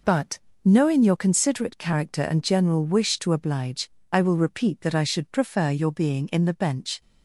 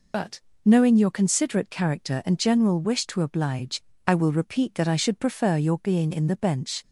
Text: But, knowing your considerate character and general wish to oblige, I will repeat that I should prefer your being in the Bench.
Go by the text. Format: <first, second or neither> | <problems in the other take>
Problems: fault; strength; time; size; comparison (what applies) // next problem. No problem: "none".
first | loses the start of "But"; at 0.1 s; 60 ms